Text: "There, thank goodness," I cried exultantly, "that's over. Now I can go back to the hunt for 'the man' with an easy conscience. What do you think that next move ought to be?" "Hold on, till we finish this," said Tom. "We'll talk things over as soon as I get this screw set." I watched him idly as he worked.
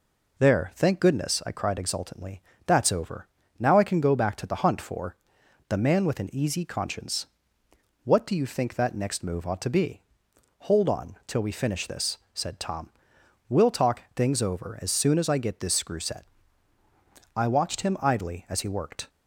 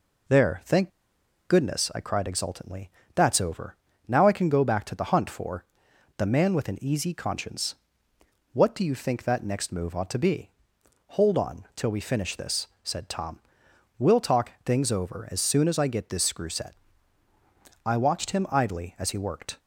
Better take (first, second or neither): first